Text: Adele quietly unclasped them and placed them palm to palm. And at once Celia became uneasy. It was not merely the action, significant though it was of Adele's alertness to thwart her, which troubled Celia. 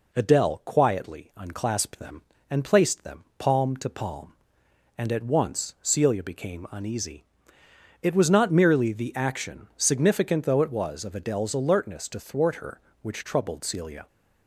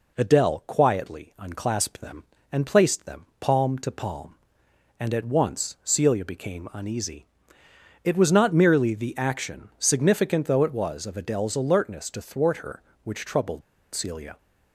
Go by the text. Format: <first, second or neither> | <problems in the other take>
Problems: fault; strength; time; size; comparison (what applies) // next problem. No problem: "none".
first | pauses between "troubled" and "Celia"; slight; at 13.6 s; 0.32 s long